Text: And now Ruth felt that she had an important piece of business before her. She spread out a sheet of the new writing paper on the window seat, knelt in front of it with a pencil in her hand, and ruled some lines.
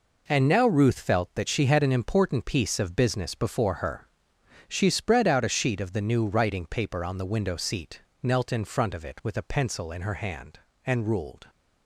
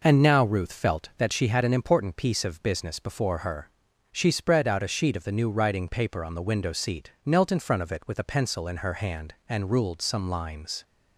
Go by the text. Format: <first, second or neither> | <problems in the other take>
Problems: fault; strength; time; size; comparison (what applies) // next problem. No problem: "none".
second | stops before "some lines"; at 11.4 s